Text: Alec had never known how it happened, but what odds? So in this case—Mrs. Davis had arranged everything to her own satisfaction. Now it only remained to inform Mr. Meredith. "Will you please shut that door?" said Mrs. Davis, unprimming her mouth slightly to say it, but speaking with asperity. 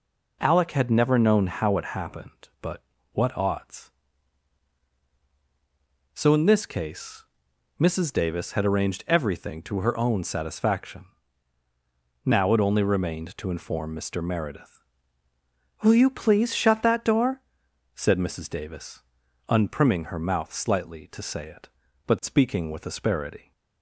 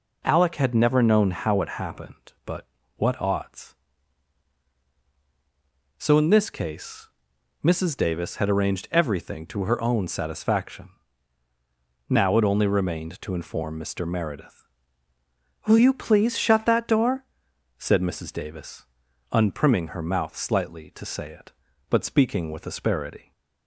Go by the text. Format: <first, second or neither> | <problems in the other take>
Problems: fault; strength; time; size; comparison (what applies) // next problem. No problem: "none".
neither | pauses between "but" and "what"; slight; the same in both